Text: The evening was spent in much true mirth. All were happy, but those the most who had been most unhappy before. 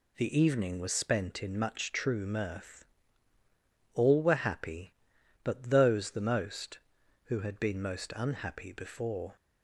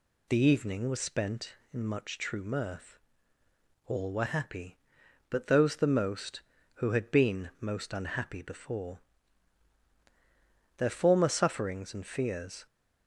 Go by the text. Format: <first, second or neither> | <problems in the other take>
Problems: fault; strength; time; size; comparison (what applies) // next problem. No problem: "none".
first | goes on to say "Their former sufferings and fears"; strong; from 10.7 s on; 1.8 s long